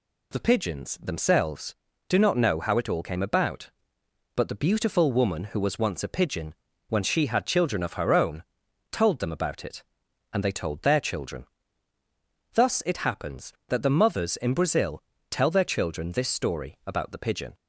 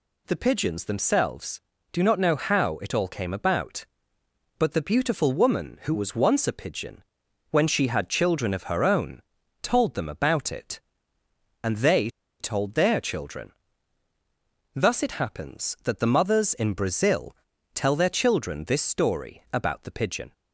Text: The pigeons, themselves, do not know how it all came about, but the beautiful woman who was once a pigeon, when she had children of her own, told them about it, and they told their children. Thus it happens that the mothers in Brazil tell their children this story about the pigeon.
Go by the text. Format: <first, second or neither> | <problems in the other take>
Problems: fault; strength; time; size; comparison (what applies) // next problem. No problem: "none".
first | pauses between "they" and "told"; slight; at 12.0 s; 0.31 s long // pauses between "Brazil" and "tell"; at 17.3 s; 0.38 s long; slight in the first